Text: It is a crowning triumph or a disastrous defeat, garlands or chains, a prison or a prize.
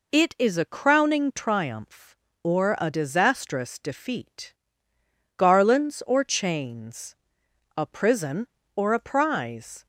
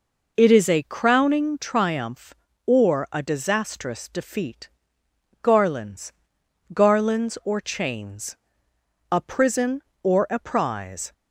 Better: first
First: none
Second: says "garlands" twice; at 6.7 s

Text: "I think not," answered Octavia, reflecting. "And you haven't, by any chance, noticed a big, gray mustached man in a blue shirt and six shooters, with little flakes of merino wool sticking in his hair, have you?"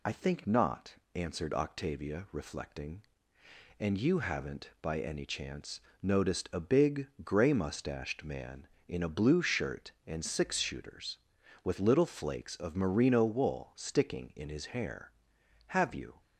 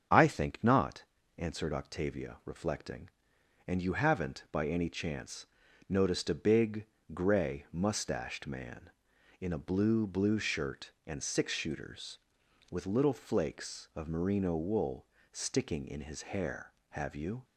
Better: first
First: none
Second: starts louder than the rest; strong; until 1.4 s; 8 dB // says "blue" twice; at 10.0 s // pauses between "wool" and "sticking"; slight; at 15.0 s; 0.26 s long // pauses between "his" and "hair"; slight; at 16.2 s; 0.16 s long

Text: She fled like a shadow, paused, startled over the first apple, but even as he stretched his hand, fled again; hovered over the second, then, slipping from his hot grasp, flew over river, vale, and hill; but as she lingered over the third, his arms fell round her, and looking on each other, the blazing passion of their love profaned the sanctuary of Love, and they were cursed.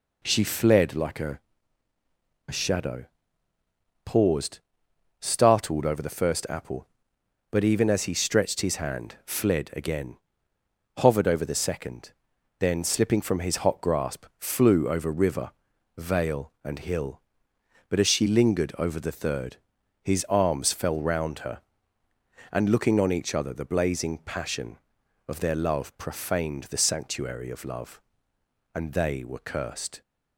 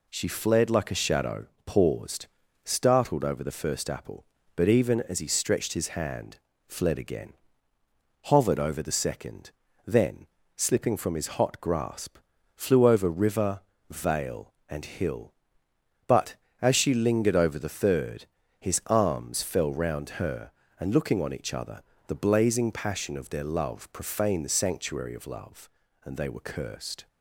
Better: second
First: says "a" twice; at 2.4 s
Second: none

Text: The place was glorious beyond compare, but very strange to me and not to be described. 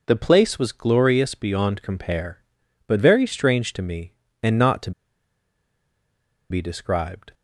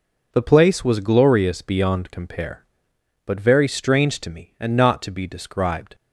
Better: second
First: pauses between "to" and "be"; strong; at 4.9 s; 1.5 s long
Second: none

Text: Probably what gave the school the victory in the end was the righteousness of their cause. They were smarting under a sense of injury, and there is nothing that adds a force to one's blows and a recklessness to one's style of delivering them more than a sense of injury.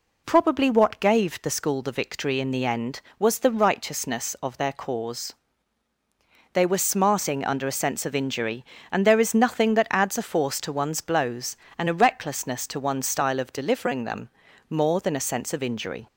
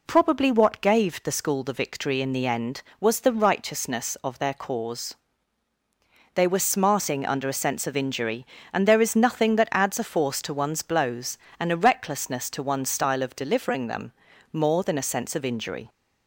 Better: neither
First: pauses between "them" and "more"; at 14.2 s; 0.40 s long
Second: pauses between "them" and "more"; at 14.1 s; 0.40 s long

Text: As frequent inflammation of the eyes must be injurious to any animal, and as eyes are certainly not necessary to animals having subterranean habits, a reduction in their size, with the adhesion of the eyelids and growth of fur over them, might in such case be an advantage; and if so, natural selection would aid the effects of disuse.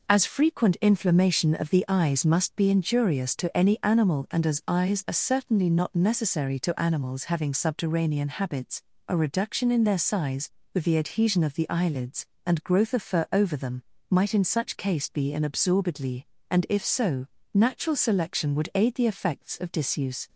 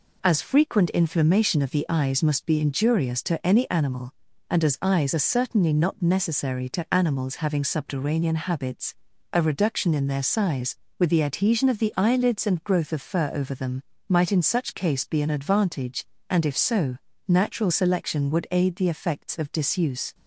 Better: second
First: says "absorbedly" for "advantage"; at 15.4 s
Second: none

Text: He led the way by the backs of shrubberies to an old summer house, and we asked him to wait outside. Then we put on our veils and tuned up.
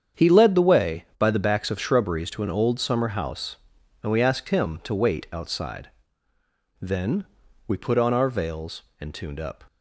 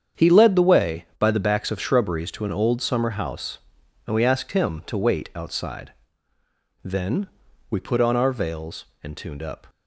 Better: neither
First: starts louder than the rest; strong; until 1.3 s; 8 dB // pauses between "Then" and "we"; at 7.2 s; 0.42 s long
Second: starts louder than the rest; strong; until 1.3 s; 8 dB // pauses between "Then" and "we"; at 7.2 s; 0.42 s long

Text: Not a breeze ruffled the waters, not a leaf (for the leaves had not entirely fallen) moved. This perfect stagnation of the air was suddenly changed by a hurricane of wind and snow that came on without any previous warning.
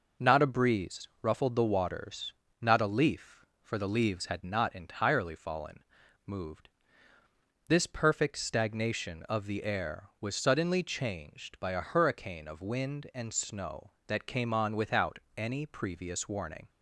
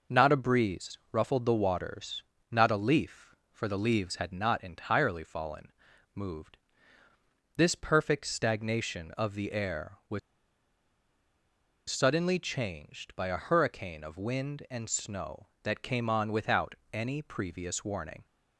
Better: first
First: pauses between "without" and "any"; slight; at 15.1 s; 0.16 s long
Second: pauses between "was" and "suddenly"; strong; at 10.1 s; 1.6 s long // pauses between "without" and "any"; slight; at 16.7 s; 0.16 s long

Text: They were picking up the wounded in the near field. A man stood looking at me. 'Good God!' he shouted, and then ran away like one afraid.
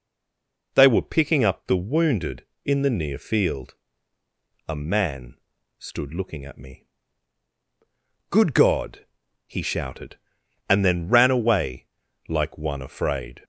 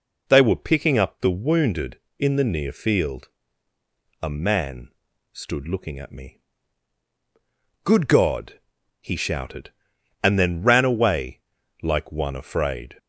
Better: second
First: stays silent before the first word; slight; until 0.7 s; 0.7 s long // pauses between "man" and "stood"; at 5.3 s; 0.44 s long // pauses between "away" and "like"; at 11.8 s; 0.40 s long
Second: pauses between "man" and "stood"; at 4.8 s; 0.44 s long // pauses between "away" and "like"; at 11.4 s; 0.40 s long

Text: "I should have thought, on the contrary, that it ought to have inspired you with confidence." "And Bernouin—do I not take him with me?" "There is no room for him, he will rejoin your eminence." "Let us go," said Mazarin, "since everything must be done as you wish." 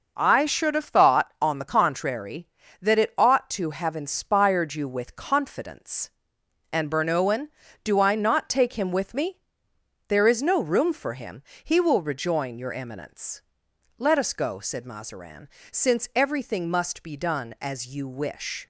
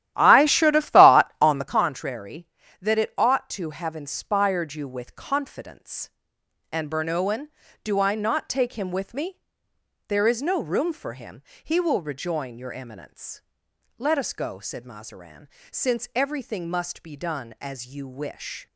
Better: first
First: none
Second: starts louder than the rest; strong; until 1.8 s; 13 dB

